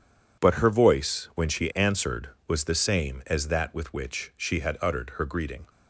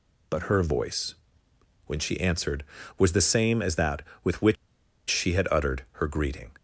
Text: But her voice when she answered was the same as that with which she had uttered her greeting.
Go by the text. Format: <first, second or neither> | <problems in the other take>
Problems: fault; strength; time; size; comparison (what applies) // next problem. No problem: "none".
first | pauses between "voice" and "when"; noticeable; at 1.1 s; 0.72 s long // pauses between "which" and "she"; noticeable; at 4.5 s; 0.54 s long